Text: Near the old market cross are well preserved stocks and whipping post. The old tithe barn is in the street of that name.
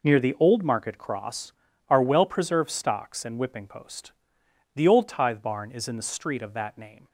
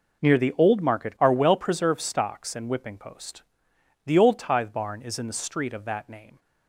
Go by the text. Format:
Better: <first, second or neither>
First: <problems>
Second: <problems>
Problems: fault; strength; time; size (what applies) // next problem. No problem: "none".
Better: first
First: none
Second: skips "cross"; at 1.1 s